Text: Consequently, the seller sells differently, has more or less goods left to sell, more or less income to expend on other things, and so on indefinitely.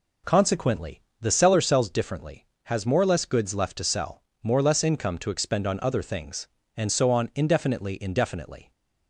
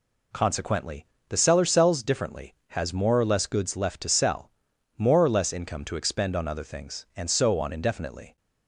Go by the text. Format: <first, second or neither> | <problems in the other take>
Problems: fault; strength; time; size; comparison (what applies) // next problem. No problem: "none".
second | says "indefinitely" twice; at 8.0 s